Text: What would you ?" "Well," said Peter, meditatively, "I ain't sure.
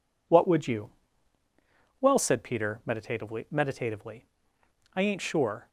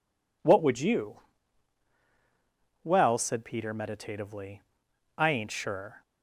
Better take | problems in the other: second | says "meditatively" twice; at 3.4 s

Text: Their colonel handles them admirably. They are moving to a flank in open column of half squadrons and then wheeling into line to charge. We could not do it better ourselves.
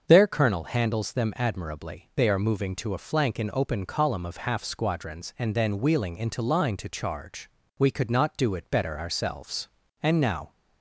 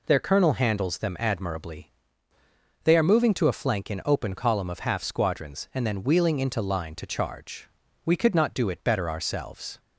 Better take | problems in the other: second | starts louder than the rest; until 1.0 s; 6.5 dB // goes on to say "And now"; from 10.0 s on; 0.50 s long

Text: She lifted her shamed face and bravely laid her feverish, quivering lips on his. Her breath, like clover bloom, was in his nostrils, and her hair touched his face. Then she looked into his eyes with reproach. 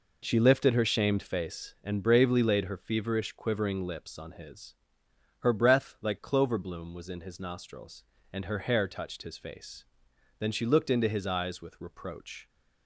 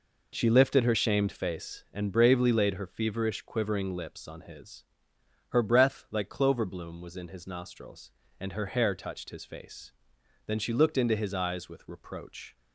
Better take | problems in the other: neither | none

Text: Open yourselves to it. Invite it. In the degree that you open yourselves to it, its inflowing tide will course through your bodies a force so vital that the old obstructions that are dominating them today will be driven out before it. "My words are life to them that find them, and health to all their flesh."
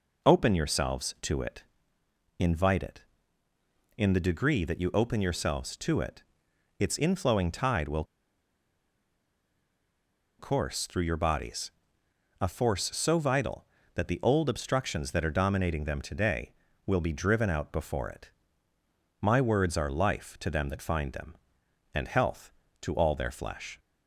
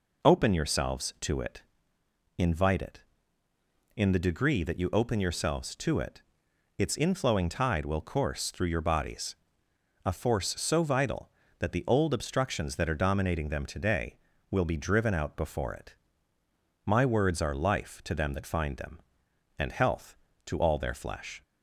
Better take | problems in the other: second | pauses between "will" and "course"; strong; at 8.0 s; 2.3 s long // pauses between "bodies" and "a"; noticeable; at 11.7 s; 0.70 s long; noticeable in the second

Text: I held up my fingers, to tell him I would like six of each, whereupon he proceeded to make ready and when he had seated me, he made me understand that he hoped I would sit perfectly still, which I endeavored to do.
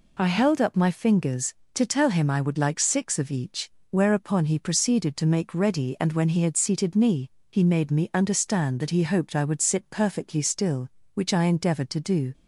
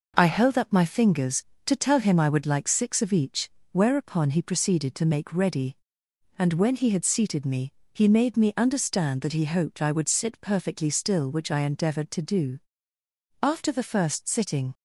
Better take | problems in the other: first | goes on to say "After the first sitting"; from 13.3 s on; 1.3 s long

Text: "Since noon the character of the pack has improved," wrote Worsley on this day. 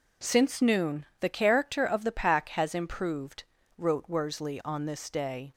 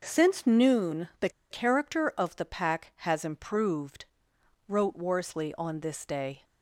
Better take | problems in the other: first | pauses between "the" and "character"; slight; at 1.2 s; 0.21 s long

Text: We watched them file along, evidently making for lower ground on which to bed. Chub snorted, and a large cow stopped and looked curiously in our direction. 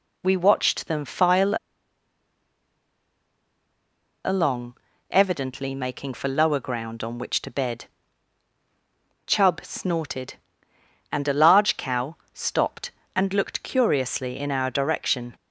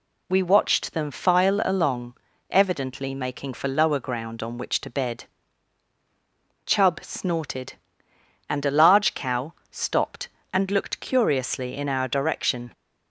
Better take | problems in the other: second | pauses between "file" and "along"; strong; at 1.5 s; 2.7 s long // pauses between "cow" and "stopped"; slight; at 12.1 s; 0.18 s long; slight in the second

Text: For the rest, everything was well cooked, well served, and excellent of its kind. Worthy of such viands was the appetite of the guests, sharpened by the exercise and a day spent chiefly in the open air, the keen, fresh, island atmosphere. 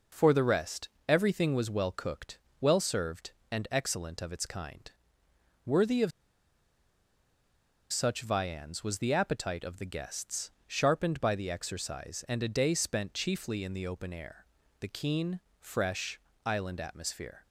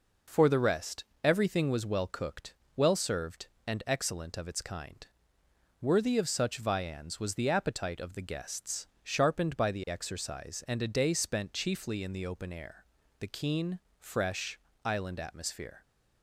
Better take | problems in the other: second | pauses between "of" and "such"; strong; at 6.1 s; 1.8 s long

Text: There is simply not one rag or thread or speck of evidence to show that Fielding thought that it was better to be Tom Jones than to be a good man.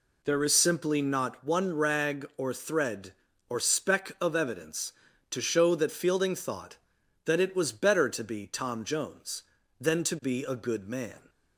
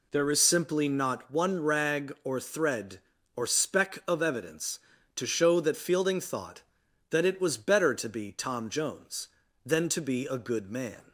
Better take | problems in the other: neither | none

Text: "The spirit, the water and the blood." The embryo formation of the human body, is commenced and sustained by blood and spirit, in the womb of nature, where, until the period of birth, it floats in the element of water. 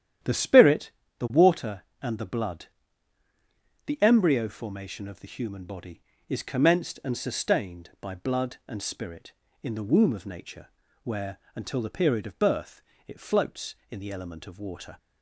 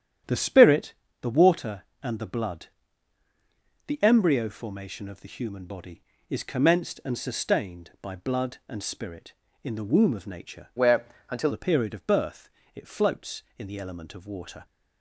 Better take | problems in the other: first | starts louder than the rest; strong; until 1.5 s; 10 dB; strong in the first // changes voice from "where" to "until"; from 10.7 to 11.5 s; 0.8 s long

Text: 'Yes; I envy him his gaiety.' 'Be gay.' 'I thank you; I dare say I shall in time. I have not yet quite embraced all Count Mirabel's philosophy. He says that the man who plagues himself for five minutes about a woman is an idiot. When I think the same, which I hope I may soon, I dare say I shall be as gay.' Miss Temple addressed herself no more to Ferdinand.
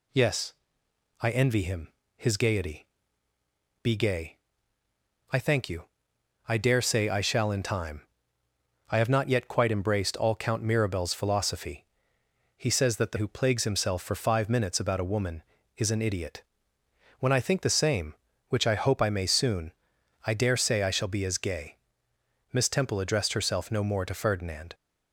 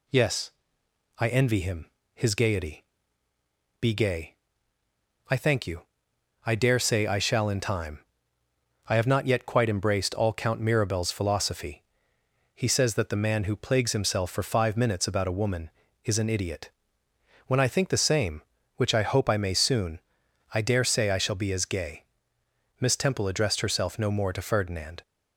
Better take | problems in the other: second | pauses between "him" and "his"; slight; at 1.9 s; 0.26 s long; slight in the second // skips "man"; at 13.1 s

